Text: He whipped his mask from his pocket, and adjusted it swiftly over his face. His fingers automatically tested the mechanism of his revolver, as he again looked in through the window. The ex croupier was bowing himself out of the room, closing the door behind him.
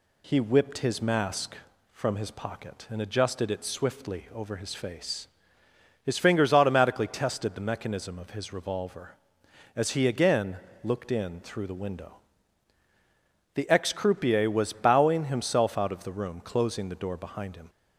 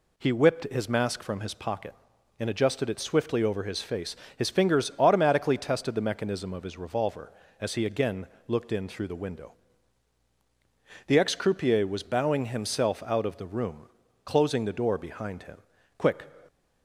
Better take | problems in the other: first | pauses between "again" and "looked"; slight; at 8.2 s; 0.22 s long; slight in the first // goes on to say "Quick"; slight; from 15.9 s on; 0.26 s long

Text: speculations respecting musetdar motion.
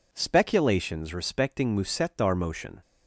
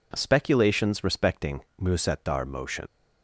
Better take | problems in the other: first | pauses between "respecting" and "musetdar"; slight; at 1.6 s; 0.18 s long // leaves "motion" unfinished; at 2.8 s; 70 ms

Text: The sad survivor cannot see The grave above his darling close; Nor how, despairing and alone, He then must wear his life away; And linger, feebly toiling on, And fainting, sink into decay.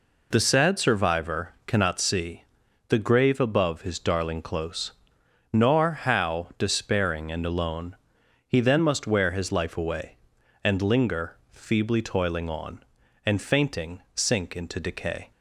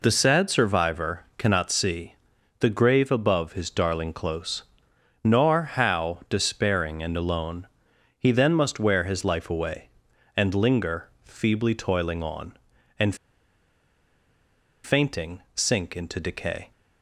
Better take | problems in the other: first | pauses between "see" and "The"; at 2.1 s; 0.44 s long; also in the first // pauses between "And" and "fainting"; strong; at 13.1 s; 1.6 s long

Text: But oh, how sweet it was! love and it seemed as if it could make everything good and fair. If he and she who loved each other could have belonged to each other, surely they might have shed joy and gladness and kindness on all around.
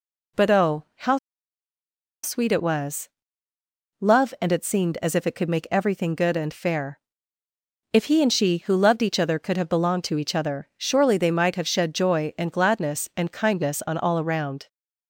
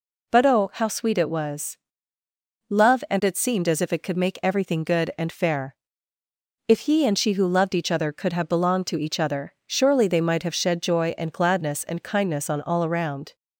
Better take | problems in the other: second | pauses between "how" and "sweet"; at 1.1 s; 1.0 s long

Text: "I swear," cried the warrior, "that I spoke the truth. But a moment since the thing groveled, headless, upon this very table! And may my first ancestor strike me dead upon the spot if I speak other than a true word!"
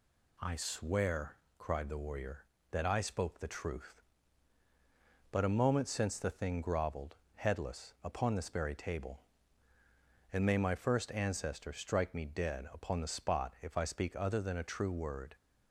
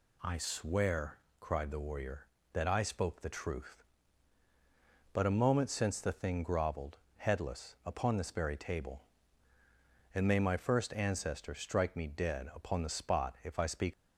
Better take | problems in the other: first | stops before "other than a true word"; at 13.9 s

